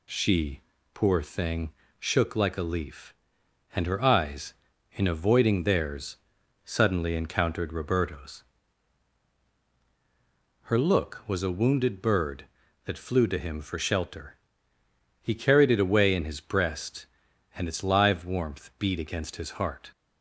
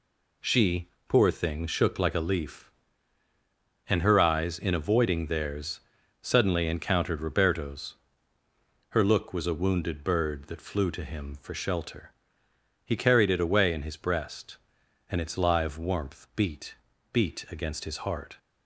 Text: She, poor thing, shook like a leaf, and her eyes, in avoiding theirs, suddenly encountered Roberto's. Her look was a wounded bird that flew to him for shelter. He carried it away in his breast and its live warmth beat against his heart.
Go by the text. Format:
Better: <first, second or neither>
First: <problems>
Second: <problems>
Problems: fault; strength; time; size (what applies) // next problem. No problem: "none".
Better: first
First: none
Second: says "beat" twice; at 17.1 s